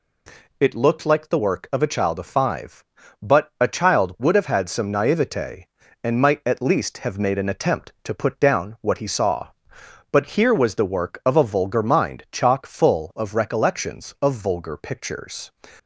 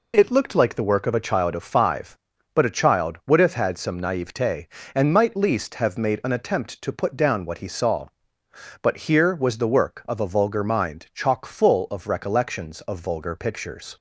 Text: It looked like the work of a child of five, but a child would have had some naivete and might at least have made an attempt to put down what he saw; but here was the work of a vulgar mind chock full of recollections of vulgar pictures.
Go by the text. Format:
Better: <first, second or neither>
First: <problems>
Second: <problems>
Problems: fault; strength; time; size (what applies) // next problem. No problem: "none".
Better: first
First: none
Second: skips "at"; at 5.3 s